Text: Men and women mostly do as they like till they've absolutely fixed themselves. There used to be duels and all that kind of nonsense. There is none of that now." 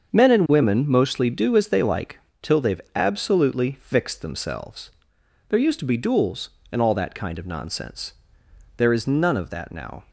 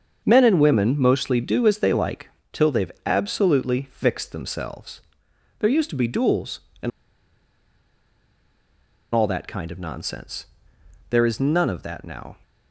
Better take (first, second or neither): first